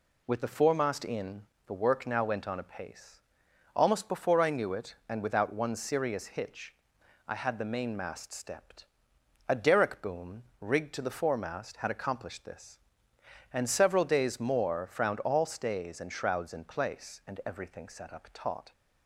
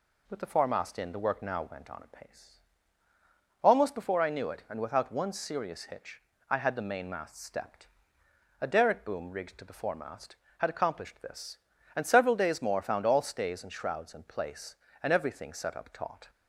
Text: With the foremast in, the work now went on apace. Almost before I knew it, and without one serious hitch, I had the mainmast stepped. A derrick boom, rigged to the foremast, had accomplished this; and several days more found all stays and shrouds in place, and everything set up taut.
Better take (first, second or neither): second